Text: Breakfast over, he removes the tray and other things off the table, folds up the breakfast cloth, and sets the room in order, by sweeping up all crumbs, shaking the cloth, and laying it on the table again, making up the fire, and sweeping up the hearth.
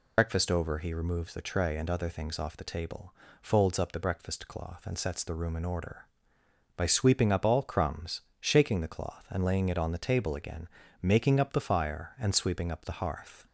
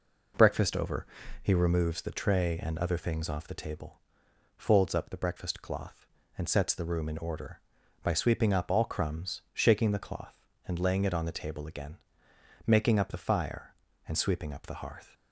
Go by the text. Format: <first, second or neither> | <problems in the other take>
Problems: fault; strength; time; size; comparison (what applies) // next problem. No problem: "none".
second | loses the start of "Breakfast"; at 0.1 s; 80 ms